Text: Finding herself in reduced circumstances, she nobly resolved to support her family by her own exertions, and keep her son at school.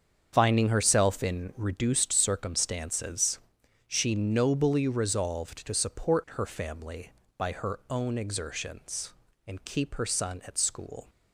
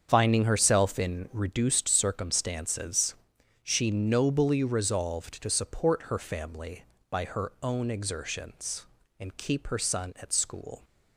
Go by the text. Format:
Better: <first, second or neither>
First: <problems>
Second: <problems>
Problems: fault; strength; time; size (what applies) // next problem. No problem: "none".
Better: neither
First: starts louder than the rest; strong; until 1.3 s; 7.5 dB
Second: starts louder than the rest; strong; until 1.1 s; 7.5 dB